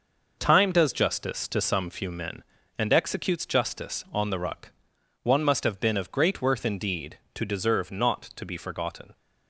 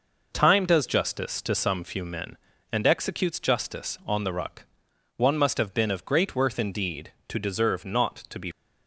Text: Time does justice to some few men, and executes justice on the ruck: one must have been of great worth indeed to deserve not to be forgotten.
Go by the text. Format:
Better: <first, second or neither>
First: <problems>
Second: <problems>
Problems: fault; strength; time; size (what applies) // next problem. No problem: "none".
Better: first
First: none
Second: stops before "forgotten"; at 8.5 s